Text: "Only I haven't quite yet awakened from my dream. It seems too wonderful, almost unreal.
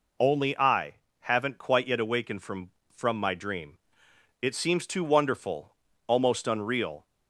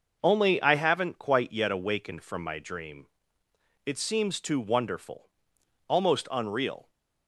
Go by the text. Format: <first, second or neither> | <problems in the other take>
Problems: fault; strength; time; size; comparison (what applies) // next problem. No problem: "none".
second | pauses between "I" and "haven't"; slight; at 0.9 s; 0.26 s long // says "from" twice; at 2.9 s